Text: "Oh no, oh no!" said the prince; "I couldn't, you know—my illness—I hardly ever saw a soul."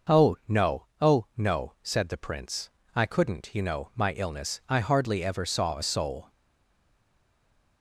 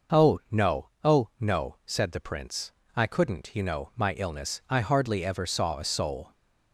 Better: second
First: stays silent after the last word; noticeable; from 6.2 s on; 1.6 s long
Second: none

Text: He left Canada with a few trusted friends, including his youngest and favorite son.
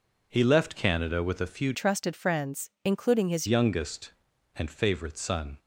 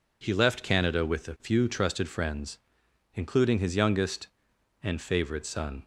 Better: second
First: changes voice from "trusted" to "his"; from 1.7 to 3.4 s; 1.7 s long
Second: none

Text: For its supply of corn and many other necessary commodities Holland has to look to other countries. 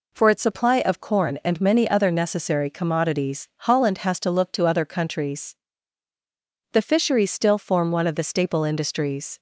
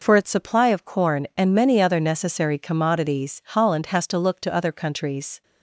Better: second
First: goes on to say "The fisheries still form one of the staple industries"; strong; from 6.7 s on; 2.6 s long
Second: none

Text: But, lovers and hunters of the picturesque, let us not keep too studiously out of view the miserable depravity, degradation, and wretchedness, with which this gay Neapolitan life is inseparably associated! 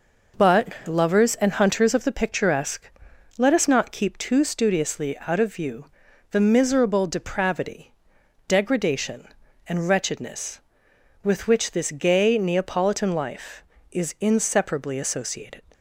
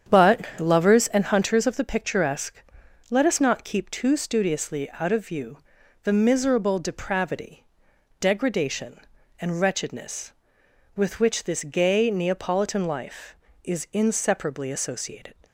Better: first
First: pauses between "view" and "the"; noticeable; at 5.8 s; 0.46 s long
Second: starts louder than the rest; strong; until 1.3 s; 8.5 dB // pauses between "view" and "the"; noticeable; at 5.5 s; 0.46 s long

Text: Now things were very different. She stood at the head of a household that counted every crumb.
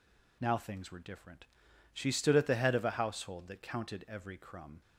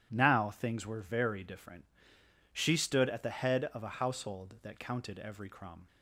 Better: second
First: skips "very"; at 0.9 s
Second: none

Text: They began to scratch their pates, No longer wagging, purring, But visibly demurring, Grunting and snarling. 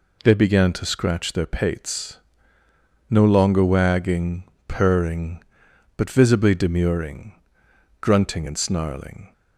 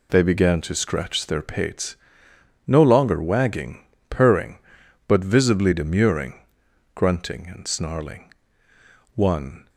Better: first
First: none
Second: goes on to say "One"; from 9.1 s on; 0.54 s long

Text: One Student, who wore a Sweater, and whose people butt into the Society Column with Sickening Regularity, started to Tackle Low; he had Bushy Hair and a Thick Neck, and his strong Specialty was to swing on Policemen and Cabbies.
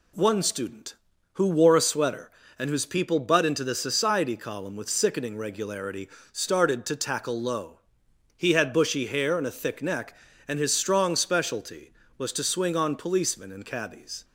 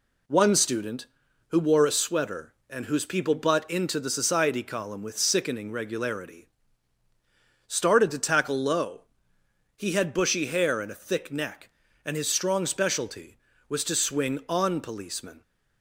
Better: first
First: none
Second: stops before "and Cabbies"; at 15.4 s

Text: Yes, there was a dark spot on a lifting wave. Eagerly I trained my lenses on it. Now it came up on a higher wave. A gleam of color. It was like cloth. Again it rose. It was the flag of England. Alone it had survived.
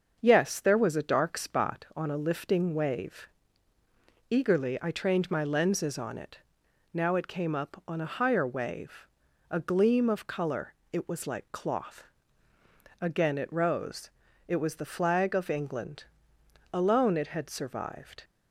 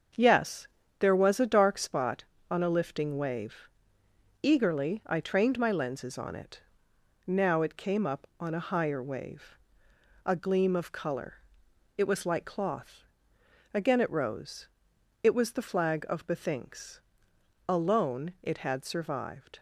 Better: first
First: starts louder than the rest; until 1.2 s; 6.5 dB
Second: starts louder than the rest; until 1.4 s; 7 dB // says "Bethinks" for "England"; at 16.2 s

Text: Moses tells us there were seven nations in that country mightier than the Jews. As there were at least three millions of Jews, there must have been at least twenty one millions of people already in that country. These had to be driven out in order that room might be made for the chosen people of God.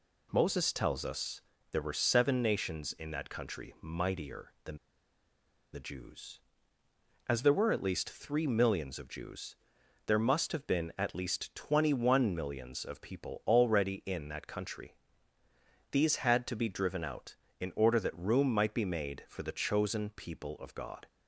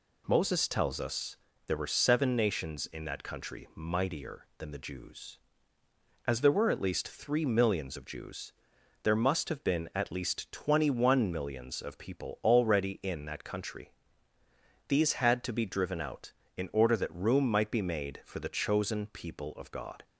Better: second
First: pauses between "us" and "there"; slight; at 1.4 s; 0.30 s long // pauses between "than" and "the"; noticeable; at 4.7 s; 0.95 s long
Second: pauses between "us" and "there"; slight; at 1.3 s; 0.30 s long

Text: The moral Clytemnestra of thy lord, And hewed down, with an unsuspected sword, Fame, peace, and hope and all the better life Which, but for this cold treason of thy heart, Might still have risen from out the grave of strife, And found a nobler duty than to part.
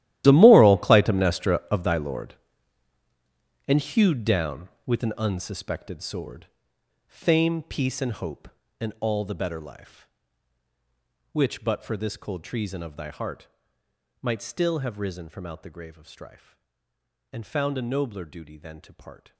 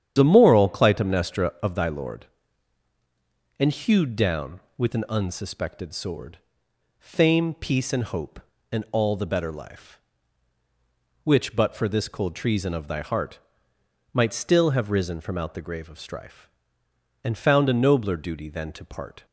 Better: second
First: gets quieter; strong; throughout; 17.5 dB // starts louder than the rest; strong; until 1.2 s; 13.5 dB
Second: starts louder than the rest; strong; until 1.1 s; 9.5 dB

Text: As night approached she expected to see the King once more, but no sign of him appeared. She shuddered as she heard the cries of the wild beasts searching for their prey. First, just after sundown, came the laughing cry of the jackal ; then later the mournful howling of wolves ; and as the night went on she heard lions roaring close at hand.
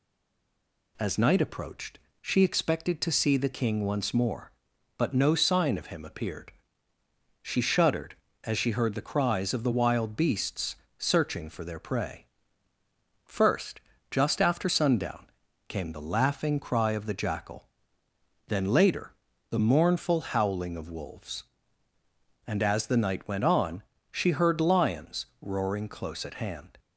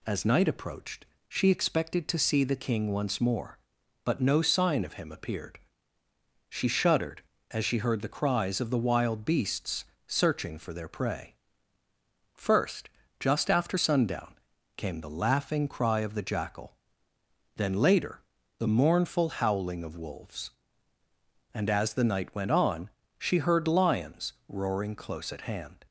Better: second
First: stays silent before the first word; slight; until 0.9 s; 0.9 s long // pauses between "approached" and "she"; slight; at 1.9 s; 0.24 s long // pauses between "beasts" and "searching"; slight; at 10.7 s; 0.22 s long // pauses between "later" and "the"; slight; at 19.1 s; 0.36 s long // pauses between "on" and "she"; slight; at 23.8 s; 0.30 s long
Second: pauses between "approached" and "she"; slight; at 1.0 s; 0.24 s long // pauses between "beasts" and "searching"; slight; at 9.8 s; 0.22 s long // pauses between "later" and "the"; slight; at 18.2 s; 0.36 s long // pauses between "on" and "she"; slight; at 22.8 s; 0.30 s long

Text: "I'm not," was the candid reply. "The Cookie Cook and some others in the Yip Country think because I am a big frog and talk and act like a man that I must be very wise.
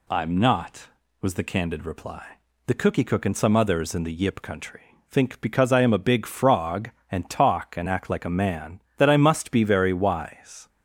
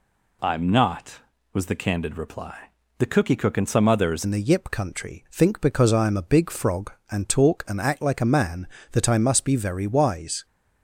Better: first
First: none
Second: changes voice at "in"; from 4.2 s on; 6.2 s long

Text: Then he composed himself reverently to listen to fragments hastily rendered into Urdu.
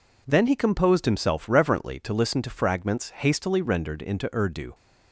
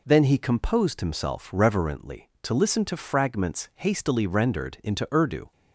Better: neither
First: none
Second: none

